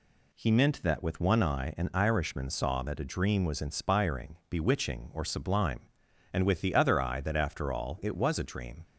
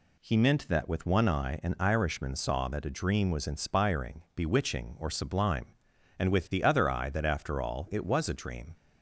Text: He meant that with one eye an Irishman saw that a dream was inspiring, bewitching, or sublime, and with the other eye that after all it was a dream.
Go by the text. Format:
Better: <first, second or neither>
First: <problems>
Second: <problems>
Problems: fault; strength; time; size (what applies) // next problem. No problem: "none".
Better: neither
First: none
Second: none